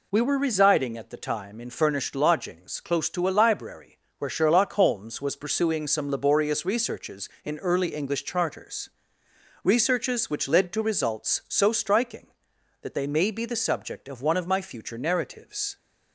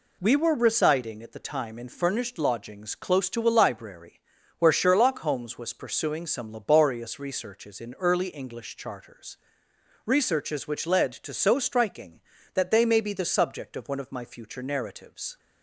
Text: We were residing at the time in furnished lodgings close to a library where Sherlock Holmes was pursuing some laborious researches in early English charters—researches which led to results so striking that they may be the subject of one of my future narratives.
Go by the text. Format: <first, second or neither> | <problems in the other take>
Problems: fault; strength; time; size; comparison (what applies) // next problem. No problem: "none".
first | pauses between "library" and "where"; at 4.1 s; 0.38 s long; slight in the first // skips "results"; at 11.3 s